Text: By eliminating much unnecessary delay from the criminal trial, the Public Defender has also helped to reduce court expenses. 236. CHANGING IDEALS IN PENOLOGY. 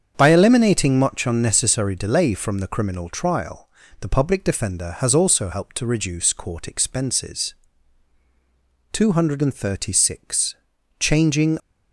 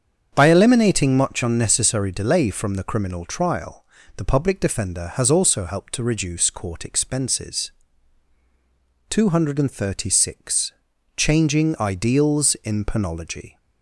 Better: second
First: starts louder than the rest; strong; until 1.1 s; 7.5 dB // stops before "IDEALS IN PENOLOGY"; at 11.5 s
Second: starts louder than the rest; strong; until 1.3 s; 7.5 dB

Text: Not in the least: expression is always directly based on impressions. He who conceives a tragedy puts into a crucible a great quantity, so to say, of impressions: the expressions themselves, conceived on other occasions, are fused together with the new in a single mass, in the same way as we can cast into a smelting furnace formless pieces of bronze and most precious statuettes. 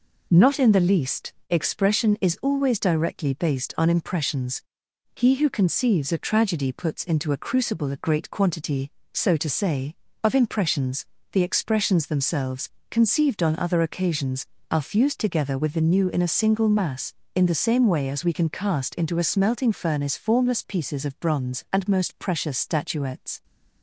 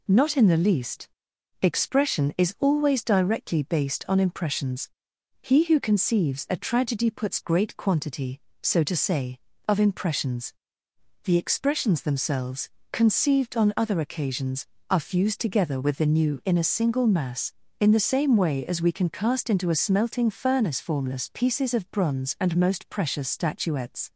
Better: first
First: none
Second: skips "into a crucible a"; at 7.4 s

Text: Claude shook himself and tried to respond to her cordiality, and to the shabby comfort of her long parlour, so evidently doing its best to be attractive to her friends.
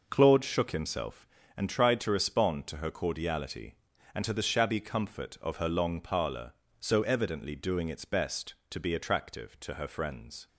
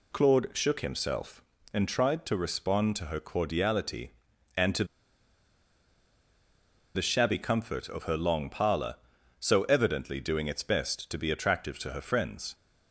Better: first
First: none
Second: pauses between "to" and "the"; strong; at 4.8 s; 2.1 s long

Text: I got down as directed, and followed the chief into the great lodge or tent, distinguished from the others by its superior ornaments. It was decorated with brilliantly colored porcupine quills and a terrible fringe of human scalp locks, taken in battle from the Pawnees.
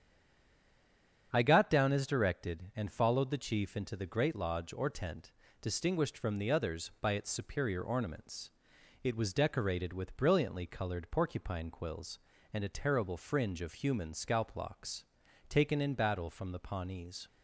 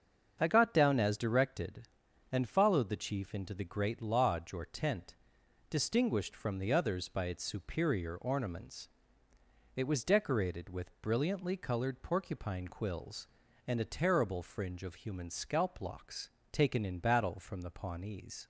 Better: second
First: stays silent before the first word; noticeable; until 1.3 s; 1.3 s long // starts louder than the rest; strong; until 2.3 s; 8.5 dB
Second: starts louder than the rest; until 1.4 s; 7 dB

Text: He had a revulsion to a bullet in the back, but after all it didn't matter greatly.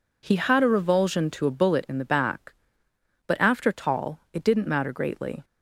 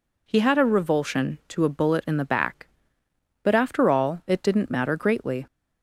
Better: second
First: says "tall" for "all"; at 3.7 s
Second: none

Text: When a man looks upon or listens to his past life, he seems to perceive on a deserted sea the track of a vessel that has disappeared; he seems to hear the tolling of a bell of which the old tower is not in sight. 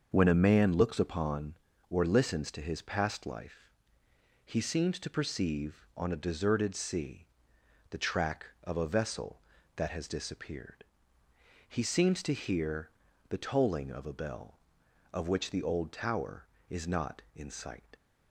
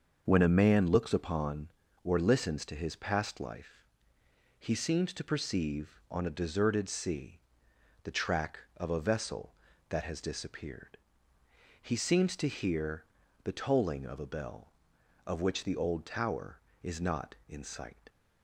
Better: neither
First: starts louder than the rest; until 1.1 s; 6.5 dB // pauses between "sea" and "the"; noticeable; at 7.2 s; 0.64 s long // pauses between "hear" and "the"; at 12.8 s; 0.40 s long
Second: starts louder than the rest; until 1.2 s; 6.5 dB // pauses between "sea" and "the"; noticeable; at 7.3 s; 0.64 s long // pauses between "hear" and "the"; at 13.0 s; 0.40 s long

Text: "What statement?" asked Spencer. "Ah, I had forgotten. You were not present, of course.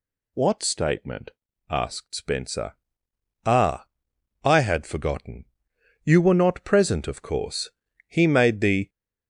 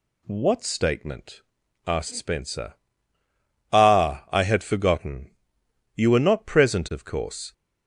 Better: second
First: goes on to say "He made the"; noticeable; from 8.0 s on; 0.80 s long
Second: none

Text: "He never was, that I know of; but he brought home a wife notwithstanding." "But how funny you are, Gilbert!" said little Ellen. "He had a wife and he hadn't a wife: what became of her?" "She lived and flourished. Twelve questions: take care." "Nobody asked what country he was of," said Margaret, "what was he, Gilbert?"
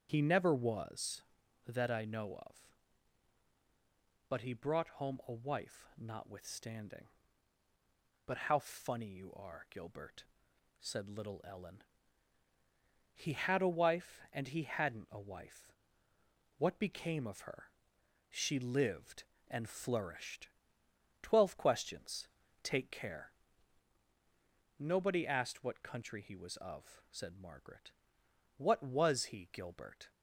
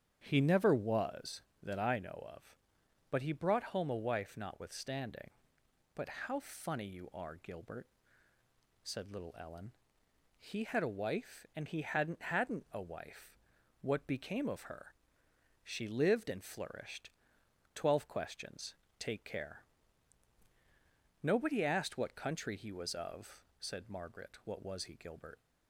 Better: first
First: none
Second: starts louder than the rest; strong; until 1.2 s; 8.5 dB // says "hadn't" twice; at 12.2 s

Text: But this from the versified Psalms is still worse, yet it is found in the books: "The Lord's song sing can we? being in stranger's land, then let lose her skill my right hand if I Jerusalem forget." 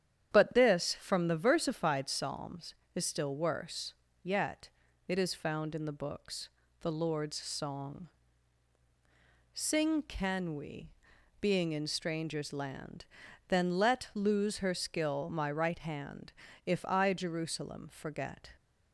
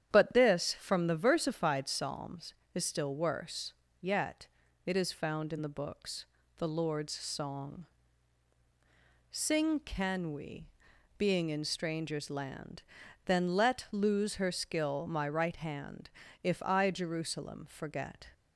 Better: neither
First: starts louder than the rest; strong; until 1.3 s; 9.5 dB // pauses between "yet" and "it"; slight; at 4.7 s; 0.36 s long // pauses between "song" and "sing"; strong; at 8.0 s; 1.4 s long // pauses between "hand" and "if"; slight; at 16.3 s; 0.34 s long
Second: starts louder than the rest; strong; until 1.1 s; 9.5 dB // pauses between "yet" and "it"; slight; at 4.4 s; 0.36 s long // pauses between "song" and "sing"; strong; at 7.8 s; 1.4 s long // pauses between "hand" and "if"; slight; at 16.0 s; 0.34 s long

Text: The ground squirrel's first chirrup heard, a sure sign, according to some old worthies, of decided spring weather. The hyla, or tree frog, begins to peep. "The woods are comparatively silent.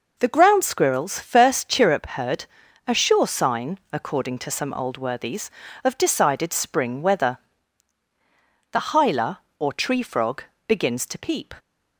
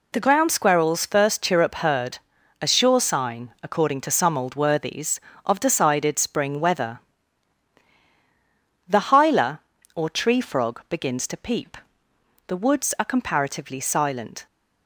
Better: second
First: stops before "The woods are comparatively silent"; at 11.5 s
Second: none

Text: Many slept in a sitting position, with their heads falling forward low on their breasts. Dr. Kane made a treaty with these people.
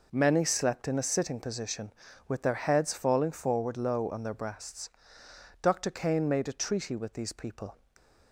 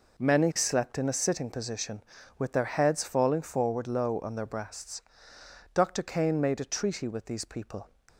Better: neither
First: none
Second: none

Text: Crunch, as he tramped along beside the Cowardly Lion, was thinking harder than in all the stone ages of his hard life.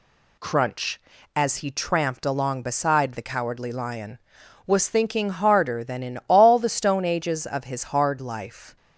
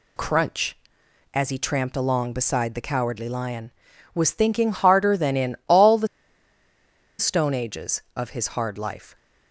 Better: first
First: none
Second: pauses between "the" and "stone"; at 6.0 s; 1.1 s long

